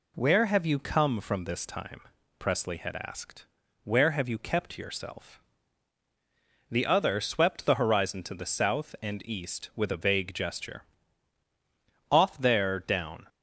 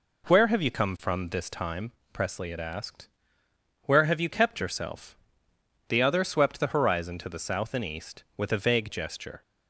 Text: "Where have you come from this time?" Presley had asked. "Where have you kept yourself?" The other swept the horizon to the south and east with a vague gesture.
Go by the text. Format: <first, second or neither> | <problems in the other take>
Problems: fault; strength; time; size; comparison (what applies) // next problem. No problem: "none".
second | goes on to say "Off there down"; noticeable; from 12.1 s on; 1.1 s long